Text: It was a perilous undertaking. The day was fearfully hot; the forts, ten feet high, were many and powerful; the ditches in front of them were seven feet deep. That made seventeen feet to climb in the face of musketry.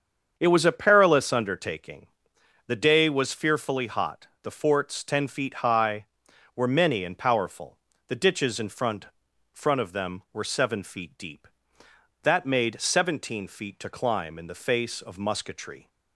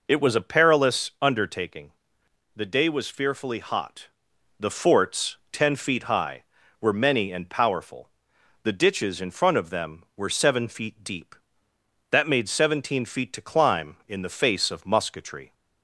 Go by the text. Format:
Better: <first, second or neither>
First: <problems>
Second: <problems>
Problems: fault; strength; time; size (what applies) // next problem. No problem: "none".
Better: second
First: starts louder than the rest; strong; until 1.3 s; 7 dB // says "front" twice; at 9.5 s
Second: none